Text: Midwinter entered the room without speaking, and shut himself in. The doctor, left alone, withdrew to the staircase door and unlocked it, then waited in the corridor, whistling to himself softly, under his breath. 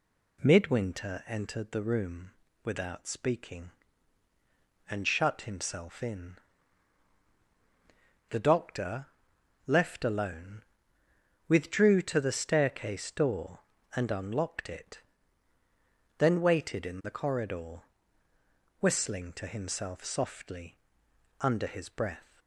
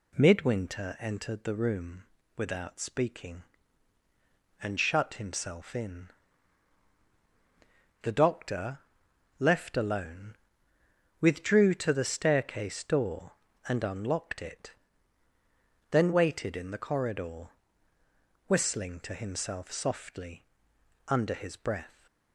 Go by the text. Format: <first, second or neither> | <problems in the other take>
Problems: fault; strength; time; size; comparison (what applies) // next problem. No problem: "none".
neither | pauses between "room" and "without"; slight; the same in both